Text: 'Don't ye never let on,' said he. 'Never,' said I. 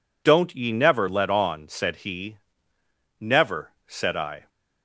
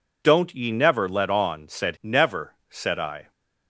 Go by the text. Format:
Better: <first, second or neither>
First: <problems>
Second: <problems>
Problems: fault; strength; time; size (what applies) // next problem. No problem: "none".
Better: first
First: none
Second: skips "he"; at 1.9 s